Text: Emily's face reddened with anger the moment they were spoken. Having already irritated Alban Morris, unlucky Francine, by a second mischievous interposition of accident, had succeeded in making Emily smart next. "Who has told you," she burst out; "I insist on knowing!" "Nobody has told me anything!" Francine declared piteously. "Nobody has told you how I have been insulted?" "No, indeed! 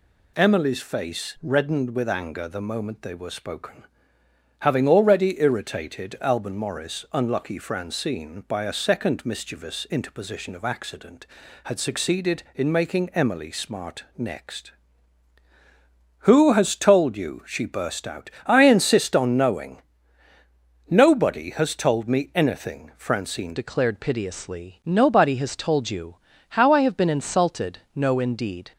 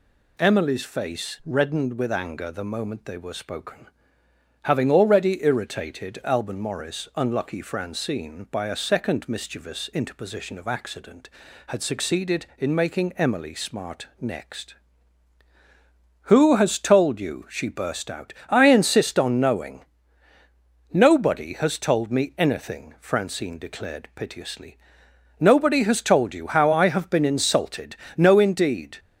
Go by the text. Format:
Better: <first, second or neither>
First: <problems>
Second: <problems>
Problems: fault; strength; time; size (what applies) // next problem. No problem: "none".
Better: second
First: changes voice at "declared"; from 23.5 s on; 5.2 s long // pauses between "you" and "how"; slight; at 26.1 s; 0.34 s long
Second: none